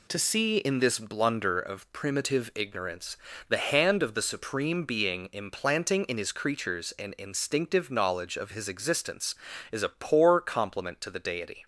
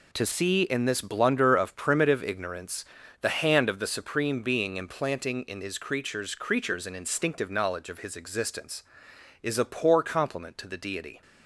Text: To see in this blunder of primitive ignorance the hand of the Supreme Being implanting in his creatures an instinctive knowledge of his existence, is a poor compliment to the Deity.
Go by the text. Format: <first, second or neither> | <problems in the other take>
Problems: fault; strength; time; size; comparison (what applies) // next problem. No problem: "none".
first | pauses between "ignorance" and "the"; at 2.8 s; 0.38 s long; slight in the first // says "creatures" twice; at 6.3 s